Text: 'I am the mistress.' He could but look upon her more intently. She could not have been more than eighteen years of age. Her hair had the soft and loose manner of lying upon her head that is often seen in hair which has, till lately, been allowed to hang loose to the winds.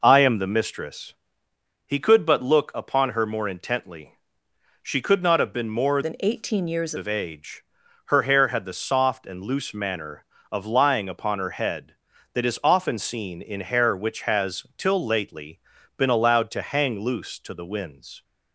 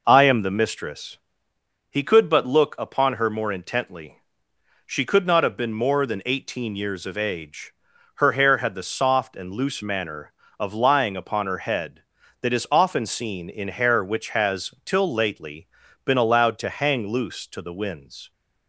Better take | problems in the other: second | changes voice from "than" to "years"; from 6.0 to 6.9 s; 0.9 s long

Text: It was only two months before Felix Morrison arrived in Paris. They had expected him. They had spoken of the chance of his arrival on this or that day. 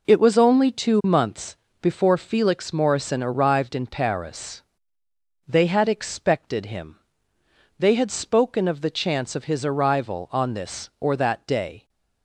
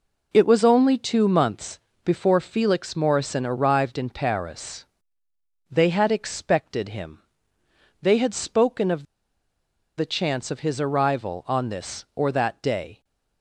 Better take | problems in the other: first | pauses between "months" and "before"; slight; at 1.7 s; 0.28 s long; slight in the first // pauses between "of" and "the"; noticeable; at 9.0 s; 0.94 s long

